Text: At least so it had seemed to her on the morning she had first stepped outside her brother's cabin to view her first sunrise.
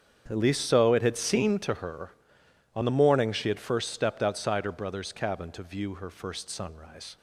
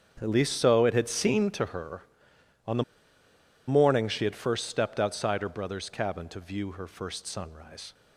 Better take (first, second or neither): first